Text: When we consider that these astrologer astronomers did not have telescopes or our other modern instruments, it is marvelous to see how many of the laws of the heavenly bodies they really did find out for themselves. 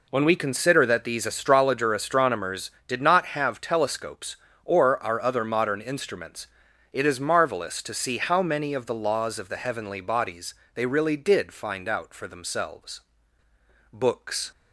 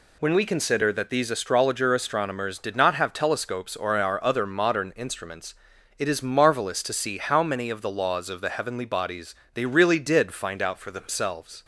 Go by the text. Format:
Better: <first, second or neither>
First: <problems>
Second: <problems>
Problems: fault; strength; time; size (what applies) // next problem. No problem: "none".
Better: second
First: pauses between "bodies" and "they"; slight; at 10.5 s; 0.22 s long // goes on to say "Books"; from 13.9 s on; 0.58 s long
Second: pauses between "bodies" and "they"; slight; at 9.3 s; 0.18 s long